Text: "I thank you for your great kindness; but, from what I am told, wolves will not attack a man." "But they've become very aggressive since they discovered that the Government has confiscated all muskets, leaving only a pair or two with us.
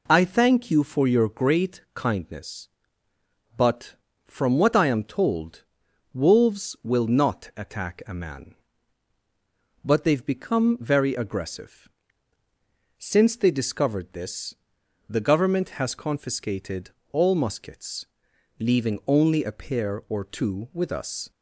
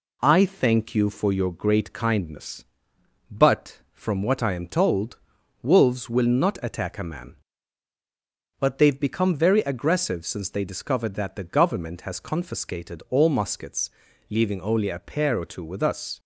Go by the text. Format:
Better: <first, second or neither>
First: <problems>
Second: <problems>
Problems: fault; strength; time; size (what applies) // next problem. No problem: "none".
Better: second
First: pauses between "aggressive" and "since"; at 11.8 s; 1.0 s long // says "this" for "that"; at 14.1 s // pauses between "confiscated" and "all"; slight; at 16.9 s; 0.20 s long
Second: none